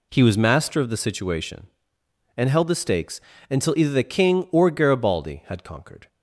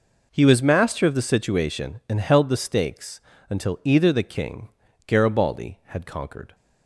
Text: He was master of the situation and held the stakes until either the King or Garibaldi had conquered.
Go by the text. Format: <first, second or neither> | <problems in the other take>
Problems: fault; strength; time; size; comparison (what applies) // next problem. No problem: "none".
first | pauses between "stakes" and "until"; slight; at 3.1 s; 0.30 s long; slight in the first // skips "or"; at 4.8 s